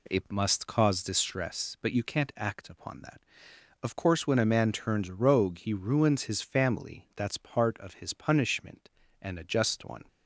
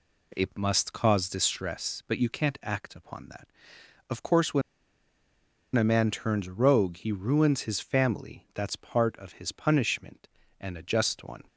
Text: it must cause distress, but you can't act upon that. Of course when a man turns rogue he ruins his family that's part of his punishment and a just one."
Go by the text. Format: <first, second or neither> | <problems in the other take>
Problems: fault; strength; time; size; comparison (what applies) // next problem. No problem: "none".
first | pauses between "when" and "a"; at 4.6 s; 1.1 s long